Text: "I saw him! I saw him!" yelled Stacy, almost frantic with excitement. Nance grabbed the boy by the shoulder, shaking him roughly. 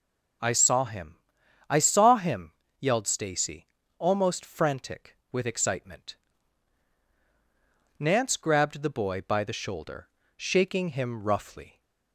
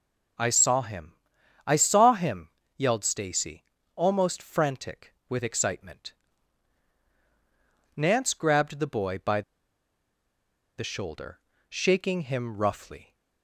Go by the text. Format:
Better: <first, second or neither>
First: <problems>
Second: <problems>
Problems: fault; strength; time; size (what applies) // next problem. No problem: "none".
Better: first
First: none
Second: pauses between "by" and "the"; strong; at 9.4 s; 1.3 s long